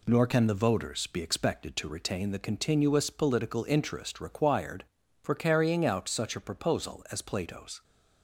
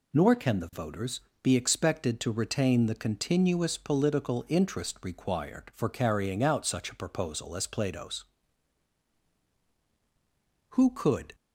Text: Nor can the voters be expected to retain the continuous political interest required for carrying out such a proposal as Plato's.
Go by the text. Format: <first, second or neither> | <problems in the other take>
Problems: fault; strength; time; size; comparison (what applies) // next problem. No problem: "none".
first | pauses between "voters" and "be"; slight; at 1.2 s; 0.22 s long // goes on to say "Who could"; noticeable; from 10.7 s on; 0.64 s long